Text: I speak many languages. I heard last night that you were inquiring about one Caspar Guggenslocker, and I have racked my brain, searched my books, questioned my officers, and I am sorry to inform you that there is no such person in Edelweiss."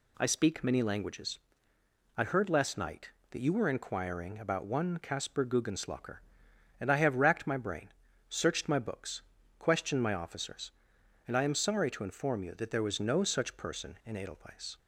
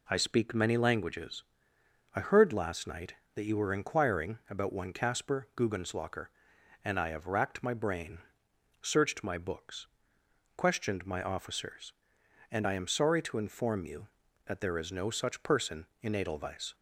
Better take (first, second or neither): second